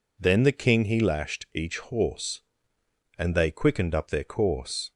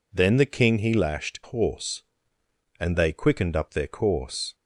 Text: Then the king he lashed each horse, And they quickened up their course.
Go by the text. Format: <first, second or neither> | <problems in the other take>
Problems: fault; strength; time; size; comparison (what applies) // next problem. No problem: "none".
first | skips "each"; at 1.4 s